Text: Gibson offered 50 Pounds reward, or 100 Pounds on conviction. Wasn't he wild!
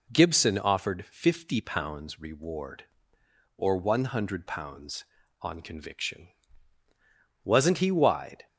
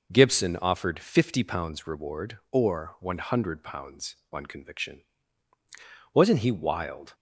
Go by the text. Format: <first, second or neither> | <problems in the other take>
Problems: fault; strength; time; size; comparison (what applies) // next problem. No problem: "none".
second | says "wide" for "wild"; at 7.9 s